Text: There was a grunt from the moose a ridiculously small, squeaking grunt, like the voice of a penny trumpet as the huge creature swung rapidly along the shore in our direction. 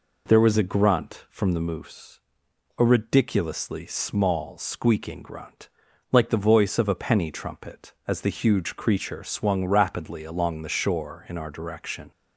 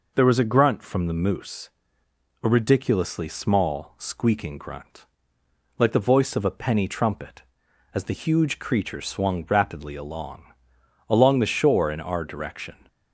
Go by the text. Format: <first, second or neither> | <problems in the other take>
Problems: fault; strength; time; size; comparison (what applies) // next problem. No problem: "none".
first | pauses between "moose" and "a"; noticeable; at 1.6 s; 0.74 s long; noticeable in the first // says "along" twice; at 11.0 s